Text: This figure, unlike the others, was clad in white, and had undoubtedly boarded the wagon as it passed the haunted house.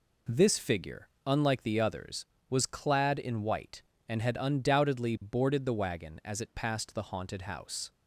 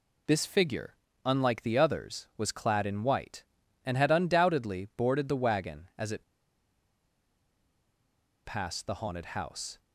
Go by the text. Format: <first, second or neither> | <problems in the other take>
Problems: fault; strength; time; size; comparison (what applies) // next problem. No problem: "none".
first | pauses between "it" and "passed"; strong; at 6.2 s; 2.2 s long